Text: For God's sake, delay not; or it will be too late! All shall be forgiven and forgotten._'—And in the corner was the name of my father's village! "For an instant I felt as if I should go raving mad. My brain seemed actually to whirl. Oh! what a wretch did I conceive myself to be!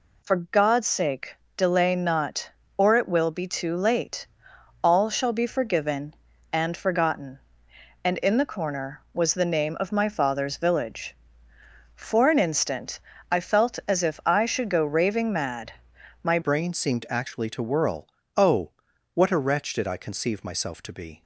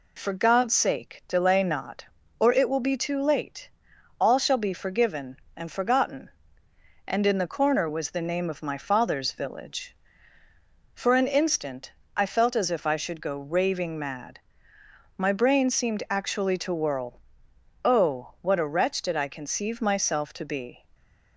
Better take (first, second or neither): second